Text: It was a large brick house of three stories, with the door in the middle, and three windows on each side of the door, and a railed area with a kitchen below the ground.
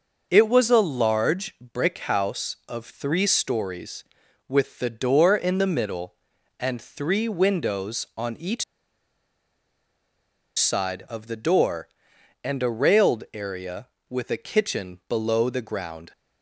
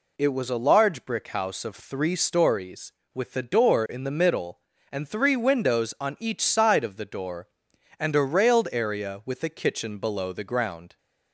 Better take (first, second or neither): second